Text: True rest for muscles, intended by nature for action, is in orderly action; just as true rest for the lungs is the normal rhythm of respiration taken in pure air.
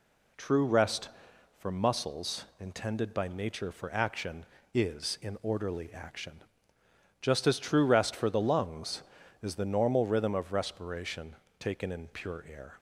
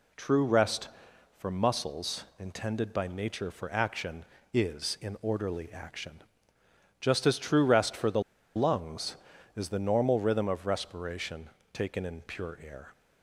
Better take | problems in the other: first | pauses between "the" and "lungs"; slight; at 8.2 s; 0.34 s long // pauses between "respiration" and "taken"; slight; at 11.4 s; 0.22 s long; slight in the first

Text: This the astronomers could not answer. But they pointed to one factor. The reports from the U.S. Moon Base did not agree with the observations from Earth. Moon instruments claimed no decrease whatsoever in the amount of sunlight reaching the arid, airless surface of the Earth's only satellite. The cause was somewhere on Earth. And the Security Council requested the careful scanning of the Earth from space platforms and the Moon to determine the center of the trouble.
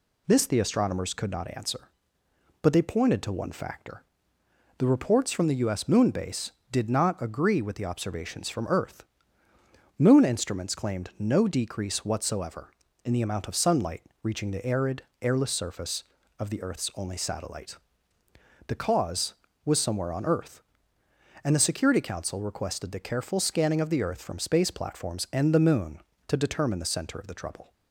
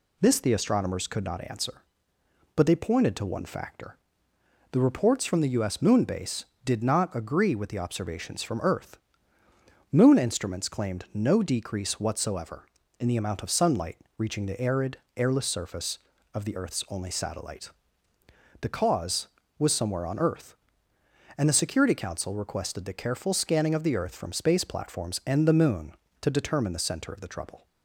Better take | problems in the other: neither | pauses between "sunlight" and "reaching"; slight; the same in both

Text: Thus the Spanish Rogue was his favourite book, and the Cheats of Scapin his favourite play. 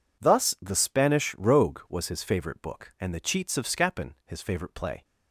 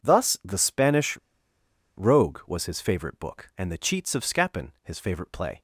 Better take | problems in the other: first | pauses between "Spanish" and "Rogue"; noticeable; at 1.1 s; 0.80 s long

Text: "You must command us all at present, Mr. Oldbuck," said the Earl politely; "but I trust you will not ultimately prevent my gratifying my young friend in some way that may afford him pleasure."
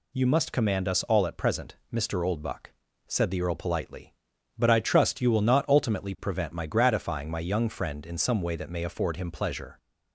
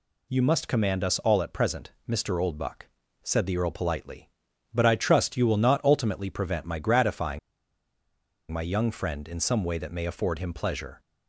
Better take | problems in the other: first | pauses between "gratifying" and "my"; at 7.3 s; 1.1 s long

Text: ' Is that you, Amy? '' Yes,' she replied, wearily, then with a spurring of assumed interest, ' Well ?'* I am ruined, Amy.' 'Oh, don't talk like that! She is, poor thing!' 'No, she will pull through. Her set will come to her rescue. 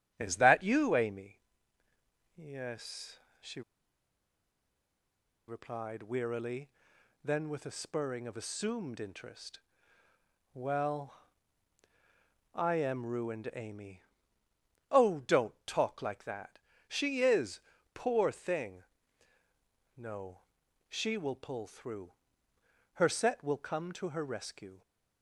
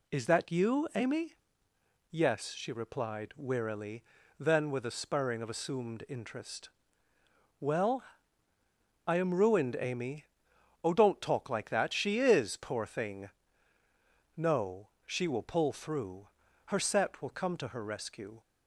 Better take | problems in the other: second | starts louder than the rest; strong; until 1.1 s; 13 dB // pauses between "she" and "replied"; strong; at 3.6 s; 1.8 s long

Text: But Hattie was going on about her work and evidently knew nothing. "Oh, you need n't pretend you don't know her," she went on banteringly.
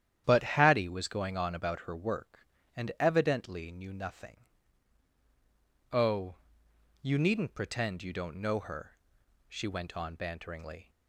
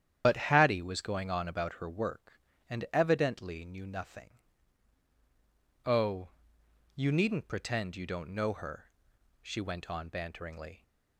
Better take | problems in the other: first | loses the start of "But"; at 0.2 s; 65 ms // starts louder than the rest; strong; until 1.2 s; 9.5 dB; strong in the first

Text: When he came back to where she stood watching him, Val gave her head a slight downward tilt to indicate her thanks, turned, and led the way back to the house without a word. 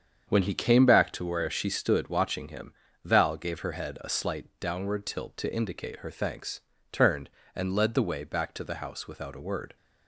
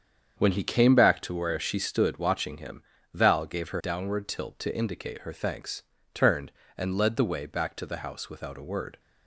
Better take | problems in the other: first | starts louder than the rest; strong; until 1.4 s; 7.5 dB; strong in the first // skips "head a slight"; at 3.8 s

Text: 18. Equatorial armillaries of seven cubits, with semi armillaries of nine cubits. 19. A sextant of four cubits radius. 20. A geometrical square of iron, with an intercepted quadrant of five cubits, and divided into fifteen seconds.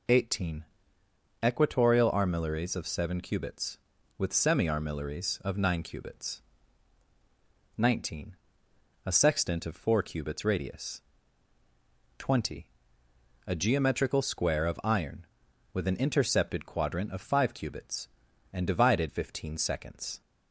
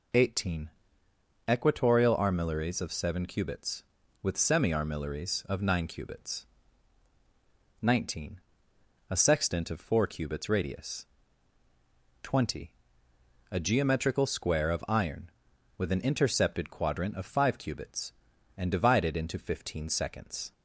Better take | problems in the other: second | skips "into"; at 19.0 s

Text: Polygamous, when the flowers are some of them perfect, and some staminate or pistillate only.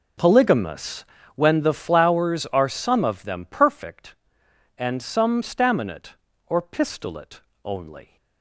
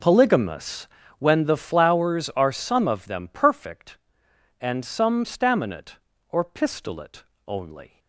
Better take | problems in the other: neither | pauses between "pistillate" and "only"; slight; the same in both

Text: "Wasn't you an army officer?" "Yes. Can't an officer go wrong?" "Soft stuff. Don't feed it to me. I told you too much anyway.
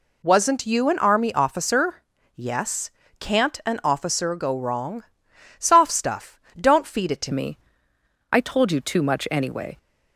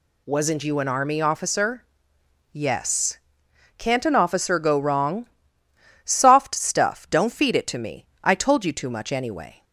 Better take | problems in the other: second | changes voice at "me"; from 7.3 s on; 2.4 s long

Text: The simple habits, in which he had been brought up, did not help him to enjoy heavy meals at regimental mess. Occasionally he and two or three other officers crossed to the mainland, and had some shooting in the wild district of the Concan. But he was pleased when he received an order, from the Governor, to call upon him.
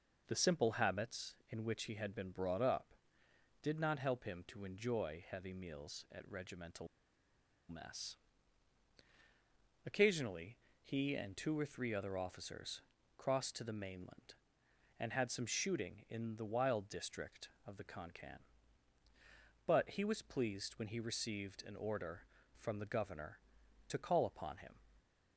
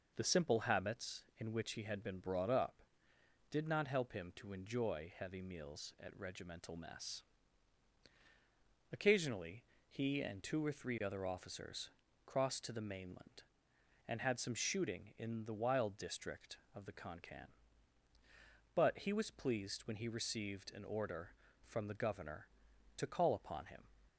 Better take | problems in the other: second | pauses between "regimental" and "mess"; noticeable; at 6.8 s; 0.82 s long // pauses between "Occasionally" and "he"; slight; at 10.5 s; 0.26 s long; slight in the second // pauses between "officers" and "crossed"; slight; at 12.8 s; 0.36 s long; slight in the second

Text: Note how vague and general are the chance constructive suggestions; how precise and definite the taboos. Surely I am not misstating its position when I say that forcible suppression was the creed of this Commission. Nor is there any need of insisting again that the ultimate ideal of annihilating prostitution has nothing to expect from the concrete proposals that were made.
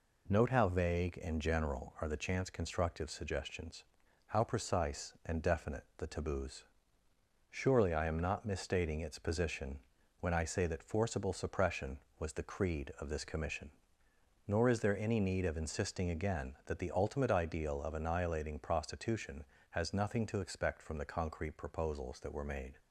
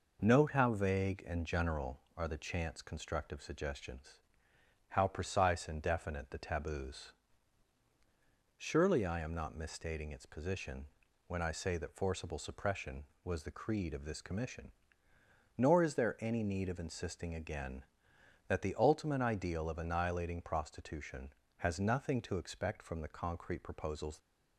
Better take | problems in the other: first | pauses between "position" and "when"; at 10.8 s; 0.42 s long; also in the first // stops before "that were made"; at 24.1 s

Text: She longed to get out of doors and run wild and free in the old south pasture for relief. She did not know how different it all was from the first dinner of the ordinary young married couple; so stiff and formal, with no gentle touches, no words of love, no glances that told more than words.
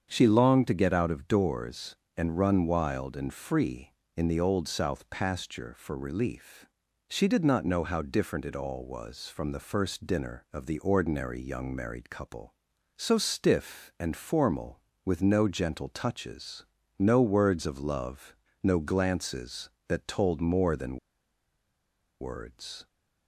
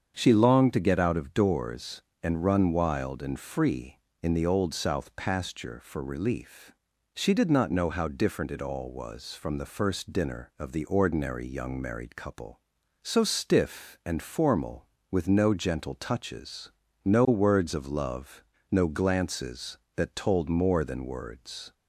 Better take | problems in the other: second | starts louder than the rest; strong; until 1.1 s; 7.5 dB; strong in the second // pauses between "than" and "words"; at 20.9 s; 1.2 s long

